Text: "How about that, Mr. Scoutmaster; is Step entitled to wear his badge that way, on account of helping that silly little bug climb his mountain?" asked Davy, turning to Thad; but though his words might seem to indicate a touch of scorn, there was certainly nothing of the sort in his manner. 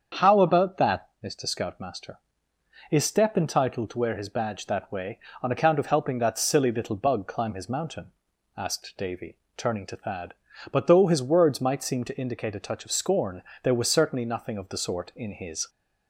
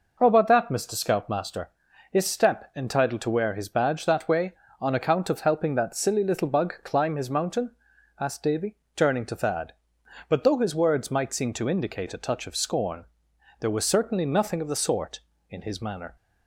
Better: second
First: starts louder than the rest; strong; until 1.3 s; 7 dB // stops before "manner"; at 15.6 s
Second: none

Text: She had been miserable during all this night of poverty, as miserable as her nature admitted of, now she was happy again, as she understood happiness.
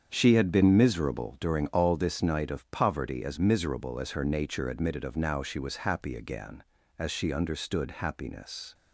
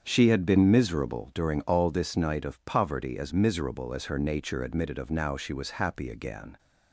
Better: first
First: starts louder than the rest; strong; until 1.1 s; 7.5 dB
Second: starts louder than the rest; strong; until 1.0 s; 7.5 dB // stops before "as she understood happiness"; at 6.5 s

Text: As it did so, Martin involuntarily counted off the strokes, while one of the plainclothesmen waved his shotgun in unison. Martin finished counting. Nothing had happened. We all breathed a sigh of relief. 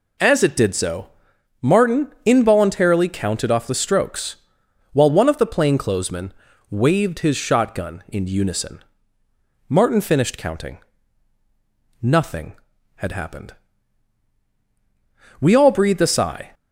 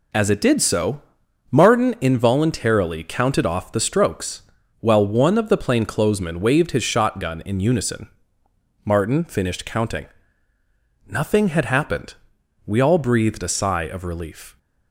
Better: second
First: pauses between "plainclothesmen" and "waved"; at 6.3 s; 0.38 s long // stops before "of relief"; at 16.5 s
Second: none

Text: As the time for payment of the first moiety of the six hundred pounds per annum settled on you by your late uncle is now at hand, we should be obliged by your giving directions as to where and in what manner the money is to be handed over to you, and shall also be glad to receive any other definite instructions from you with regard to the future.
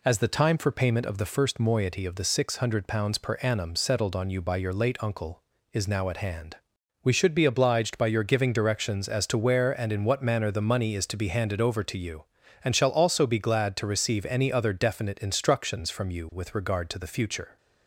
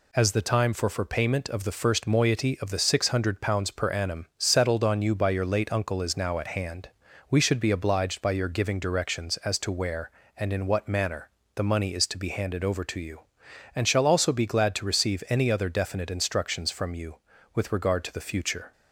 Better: first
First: none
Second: says "for" twice; at 0.8 s // pauses between "manner" and "the"; slight; at 11.2 s; 0.28 s long

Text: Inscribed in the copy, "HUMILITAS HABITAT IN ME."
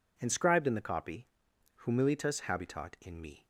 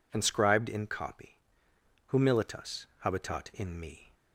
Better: first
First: none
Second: skips "the"; at 0.8 s // pauses between "HUMILITAS" and "HABITAT"; slight; at 2.8 s; 0.16 s long

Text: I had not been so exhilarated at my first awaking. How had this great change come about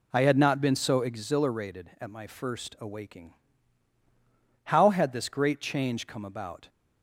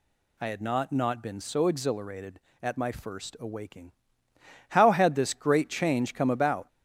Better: first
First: none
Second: says "not" twice; at 0.9 s

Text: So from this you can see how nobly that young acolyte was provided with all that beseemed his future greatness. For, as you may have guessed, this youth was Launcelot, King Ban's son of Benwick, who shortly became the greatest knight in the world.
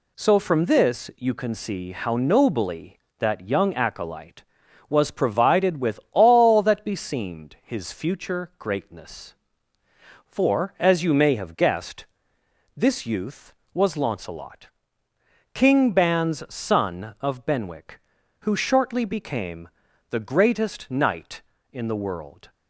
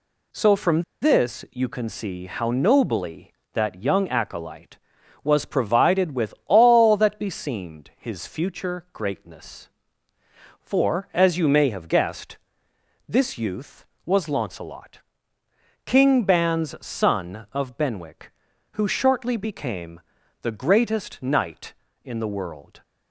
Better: first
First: pauses between "became" and "the"; at 19.6 s; 0.42 s long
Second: pauses between "from" and "this"; slight; at 0.8 s; 0.20 s long // pauses between "became" and "the"; at 19.9 s; 0.42 s long

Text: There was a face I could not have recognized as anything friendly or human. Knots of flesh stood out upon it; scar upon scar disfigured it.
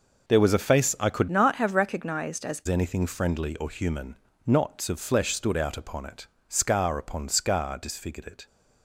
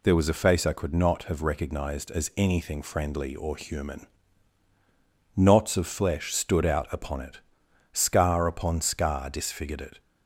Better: second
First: changes voice from "not" to "as"; from 1.3 to 2.6 s; 1.3 s long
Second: none

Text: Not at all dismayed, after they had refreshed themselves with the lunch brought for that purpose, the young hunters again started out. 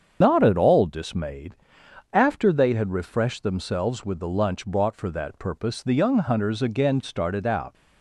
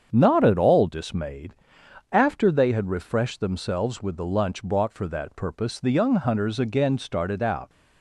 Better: second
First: loses the start of "Not"; at 0.2 s; 95 ms // starts louder than the rest; strong; until 1.2 s; 7.5 dB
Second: starts louder than the rest; strong; until 1.1 s; 7.5 dB

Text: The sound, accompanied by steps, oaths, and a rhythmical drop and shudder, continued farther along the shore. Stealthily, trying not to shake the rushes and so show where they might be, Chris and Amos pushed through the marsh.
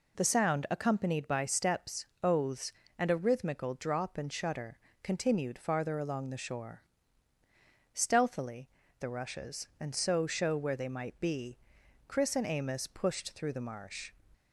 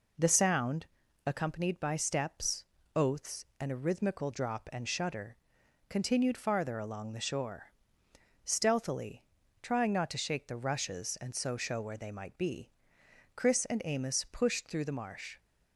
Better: second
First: skips "trying not to shake"; at 8.8 s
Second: none

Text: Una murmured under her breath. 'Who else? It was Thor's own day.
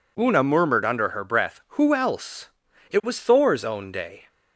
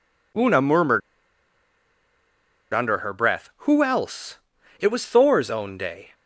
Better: first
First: none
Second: pauses between "murmured" and "under"; strong; at 1.0 s; 1.7 s long

